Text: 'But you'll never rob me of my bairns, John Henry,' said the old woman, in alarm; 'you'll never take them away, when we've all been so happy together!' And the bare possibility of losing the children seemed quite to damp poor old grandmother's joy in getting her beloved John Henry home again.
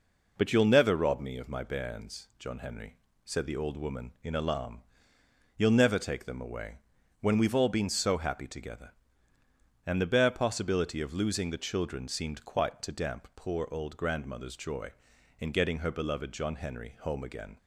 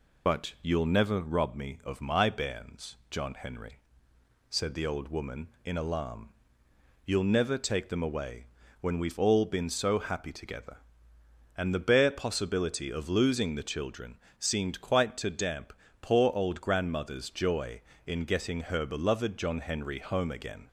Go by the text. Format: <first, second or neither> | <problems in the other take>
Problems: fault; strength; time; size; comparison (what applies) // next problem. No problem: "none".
first | loses the start of "But"; at 0.2 s; 40 ms // pauses between "children" and "seemed"; slight; at 14.1 s; 0.20 s long // pauses between "damp" and "poor"; slight; at 15.7 s; 0.28 s long